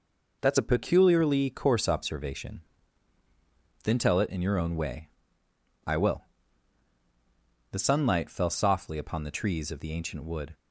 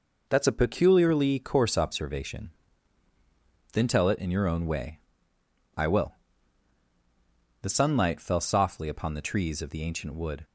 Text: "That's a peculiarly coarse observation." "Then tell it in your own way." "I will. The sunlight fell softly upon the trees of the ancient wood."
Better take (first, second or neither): neither